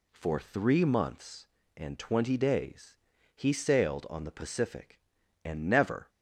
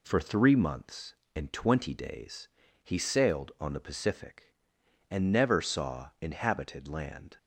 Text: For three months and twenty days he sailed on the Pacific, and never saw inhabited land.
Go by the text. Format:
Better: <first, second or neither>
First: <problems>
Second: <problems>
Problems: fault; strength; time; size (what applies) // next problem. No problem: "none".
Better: second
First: pauses between "days" and "he"; at 2.9 s; 0.38 s long // stops before "saw inhabited land"; at 6.0 s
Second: pauses between "days" and "he"; slight; at 2.4 s; 0.36 s long